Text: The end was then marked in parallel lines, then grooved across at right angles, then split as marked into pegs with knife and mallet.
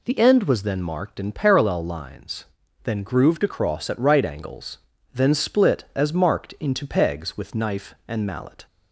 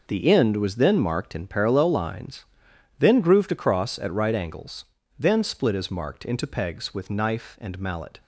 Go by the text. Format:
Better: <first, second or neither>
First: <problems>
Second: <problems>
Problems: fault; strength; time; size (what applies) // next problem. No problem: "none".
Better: first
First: none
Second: gets quieter; strong; throughout; 10.5 dB